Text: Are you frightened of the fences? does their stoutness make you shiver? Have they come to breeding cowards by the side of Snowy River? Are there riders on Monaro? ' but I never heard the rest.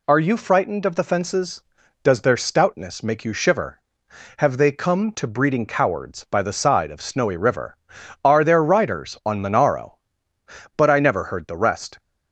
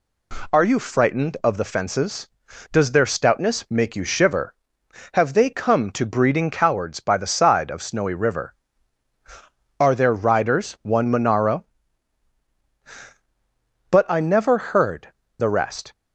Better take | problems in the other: first | says "one" for "on"; at 10.7 s // pauses between "heard" and "the"; slight; at 15.1 s; 0.24 s long

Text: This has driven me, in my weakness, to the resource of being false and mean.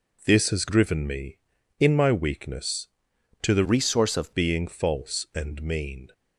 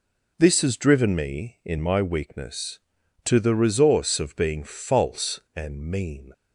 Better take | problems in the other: second | changes voice from "resource" to "of"; from 3.6 to 4.3 s; 0.7 s long

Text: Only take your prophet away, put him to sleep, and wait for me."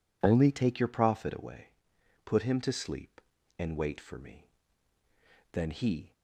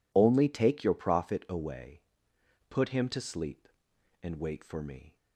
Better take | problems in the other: second | goes on to say "Then he"; from 5.5 s on; 0.60 s long

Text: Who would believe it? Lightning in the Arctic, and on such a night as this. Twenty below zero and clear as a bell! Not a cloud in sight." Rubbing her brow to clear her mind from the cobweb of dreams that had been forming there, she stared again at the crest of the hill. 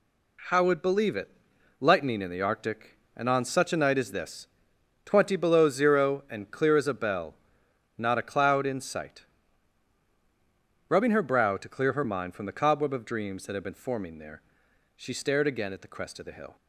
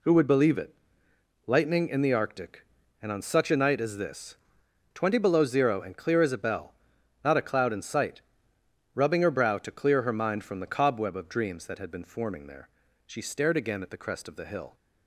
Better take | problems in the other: second | says "How" for "Who"; at 0.4 s

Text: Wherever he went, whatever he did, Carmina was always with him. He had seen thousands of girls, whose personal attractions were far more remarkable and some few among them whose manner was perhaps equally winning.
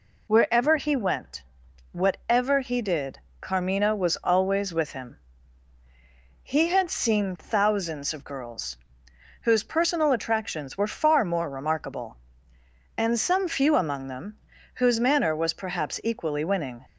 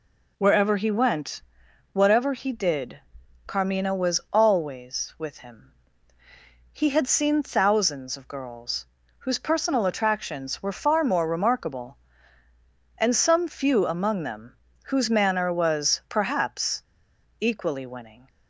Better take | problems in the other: first | pauses between "them" and "whose"; slight; at 14.5 s; 0.26 s long; slight in the first // pauses between "perhaps" and "equally"; noticeable; at 16.8 s; 0.56 s long

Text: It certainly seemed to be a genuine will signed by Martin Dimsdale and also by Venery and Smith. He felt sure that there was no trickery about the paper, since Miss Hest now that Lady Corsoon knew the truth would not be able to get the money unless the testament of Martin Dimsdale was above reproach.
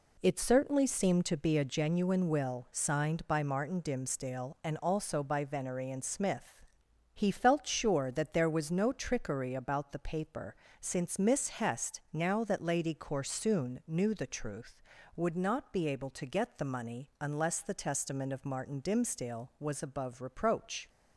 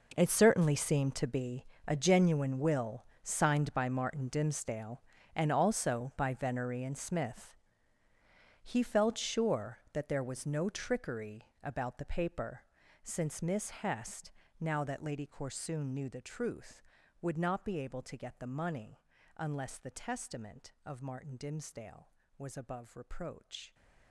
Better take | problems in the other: first | gets quieter; strong; throughout; 16 dB // pauses between "be" and "a"; slight; at 1.6 s; 0.22 s long // pauses between "will" and "signed"; slight; at 3.0 s; 0.18 s long // pauses between "Hest" and "now"; slight; at 14.3 s; 0.30 s long // pauses between "money" and "unless"; at 18.9 s; 0.38 s long

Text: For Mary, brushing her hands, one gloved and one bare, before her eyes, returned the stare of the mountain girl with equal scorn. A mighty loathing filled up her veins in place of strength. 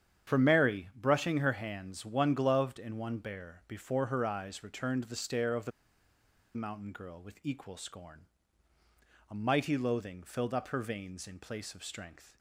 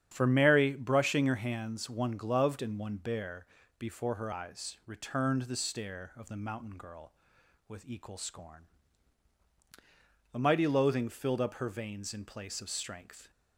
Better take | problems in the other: second | starts louder than the rest; strong; until 1.3 s; 9 dB; strong in the second // pauses between "the" and "mountain"; noticeable; at 5.7 s; 0.85 s long

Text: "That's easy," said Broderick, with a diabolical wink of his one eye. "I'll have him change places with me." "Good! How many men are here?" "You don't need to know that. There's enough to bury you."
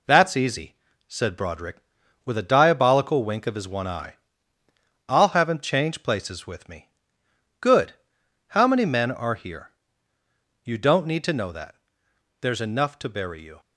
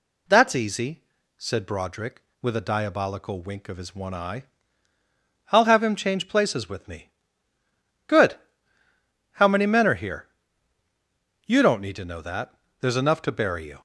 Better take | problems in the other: second | gets quieter; noticeable; throughout; 5 dB

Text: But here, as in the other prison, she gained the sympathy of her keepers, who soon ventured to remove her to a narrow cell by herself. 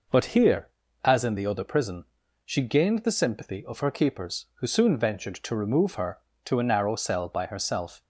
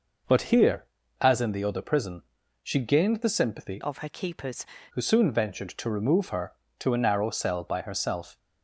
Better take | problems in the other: first | changes voice from "of" to "keepers"; from 3.8 to 4.6 s; 0.8 s long

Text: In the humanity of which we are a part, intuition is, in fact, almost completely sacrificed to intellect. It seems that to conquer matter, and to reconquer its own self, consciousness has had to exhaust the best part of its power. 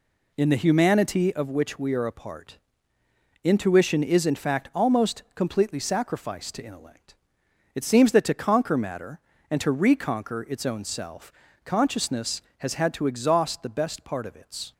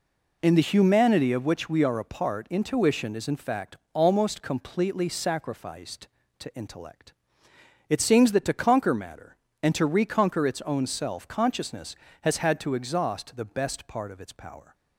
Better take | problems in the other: second | stops before "power"; at 14.7 s

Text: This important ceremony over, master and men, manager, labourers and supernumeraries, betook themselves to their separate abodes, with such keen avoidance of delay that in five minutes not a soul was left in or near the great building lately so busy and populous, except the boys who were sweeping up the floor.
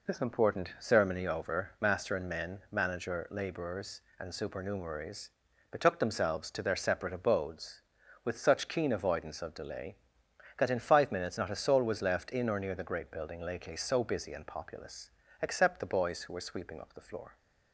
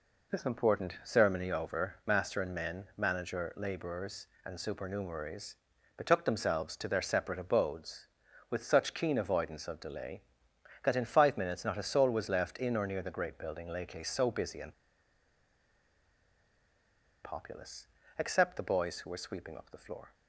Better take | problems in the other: first | pauses between "and" and "populous"; strong; at 14.7 s; 2.5 s long

